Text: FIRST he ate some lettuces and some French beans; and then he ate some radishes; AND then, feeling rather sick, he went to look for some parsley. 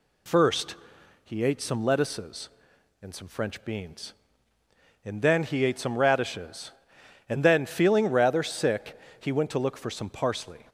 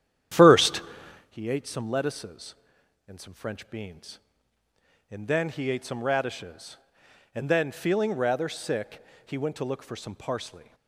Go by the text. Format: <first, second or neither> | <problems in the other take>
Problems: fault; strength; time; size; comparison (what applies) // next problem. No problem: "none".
first | starts louder than the rest; strong; until 1.4 s; 10 dB // pauses between "FIRST" and "he"; noticeable; at 0.8 s; 0.48 s long; noticeable in the first